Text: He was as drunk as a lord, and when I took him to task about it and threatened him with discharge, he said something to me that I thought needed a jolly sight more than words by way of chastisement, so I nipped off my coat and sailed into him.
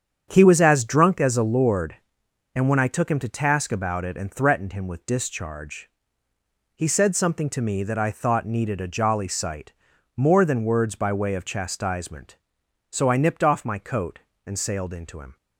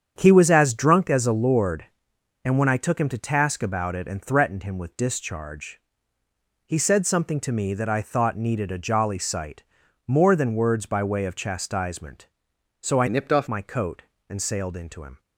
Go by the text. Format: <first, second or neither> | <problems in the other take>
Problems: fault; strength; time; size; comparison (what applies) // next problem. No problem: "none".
first | starts louder than the rest; strong; until 1.1 s; 8 dB; strong in the first // pauses between "sight" and "more"; noticeable; at 9.6 s; 0.46 s long; noticeable in the first // changes voice from "nipped" to "off"; from 13.0 to 13.4 s; 0.4 s long